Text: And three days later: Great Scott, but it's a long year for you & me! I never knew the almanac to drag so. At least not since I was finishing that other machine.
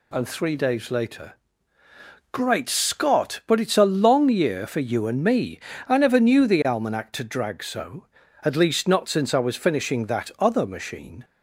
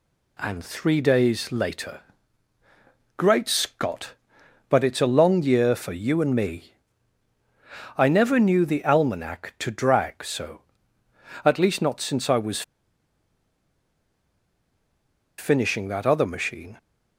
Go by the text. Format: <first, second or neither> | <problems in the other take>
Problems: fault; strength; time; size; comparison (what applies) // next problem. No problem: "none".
first | pauses between "was" and "finishing"; strong; at 12.6 s; 2.7 s long